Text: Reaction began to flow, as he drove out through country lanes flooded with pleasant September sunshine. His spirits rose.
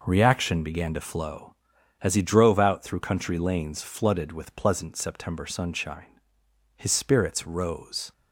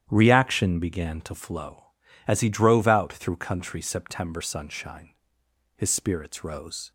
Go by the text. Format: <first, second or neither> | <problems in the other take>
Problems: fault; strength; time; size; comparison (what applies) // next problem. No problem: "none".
first | starts louder than the rest; strong; until 1.1 s; 10 dB // skips "lanes flooded with pleasant"; at 3.8 s